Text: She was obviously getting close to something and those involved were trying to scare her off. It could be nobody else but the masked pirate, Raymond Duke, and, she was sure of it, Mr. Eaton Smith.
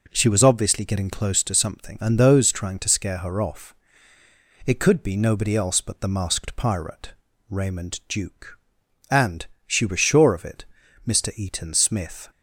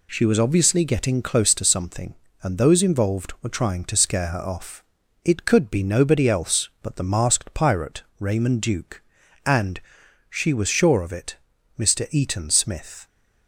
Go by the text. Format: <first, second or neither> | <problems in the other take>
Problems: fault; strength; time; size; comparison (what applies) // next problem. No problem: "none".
second | skips "involved were"; at 2.5 s